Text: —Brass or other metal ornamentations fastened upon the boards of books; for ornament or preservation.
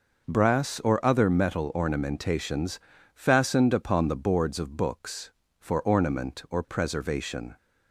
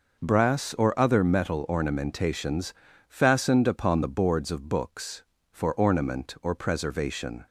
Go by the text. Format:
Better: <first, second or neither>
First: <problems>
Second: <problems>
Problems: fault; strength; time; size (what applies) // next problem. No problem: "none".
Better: neither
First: pauses between "ornamentations" and "fastened"; slight; at 2.7 s; 0.34 s long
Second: pauses between "ornamentations" and "fastened"; slight; at 2.7 s; 0.34 s long